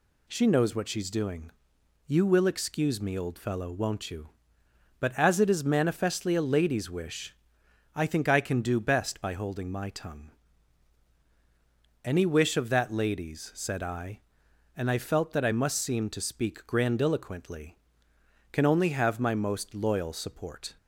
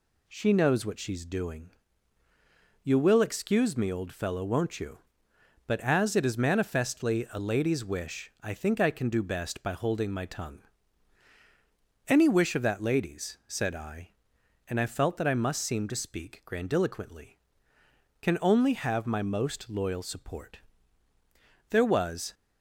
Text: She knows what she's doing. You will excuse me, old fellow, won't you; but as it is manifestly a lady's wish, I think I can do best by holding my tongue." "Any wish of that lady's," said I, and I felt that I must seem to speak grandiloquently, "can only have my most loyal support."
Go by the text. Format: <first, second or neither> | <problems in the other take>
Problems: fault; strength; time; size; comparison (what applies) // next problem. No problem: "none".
first | goes on to say "There was"; noticeable; from 21.6 s on; 0.64 s long